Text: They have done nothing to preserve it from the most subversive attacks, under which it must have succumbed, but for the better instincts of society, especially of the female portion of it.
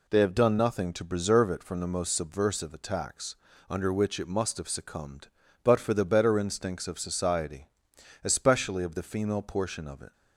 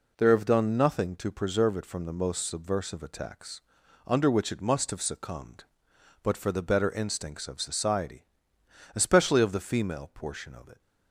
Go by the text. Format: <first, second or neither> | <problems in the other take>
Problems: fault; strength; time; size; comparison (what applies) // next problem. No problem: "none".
first | says "There" for "They"; at 0.1 s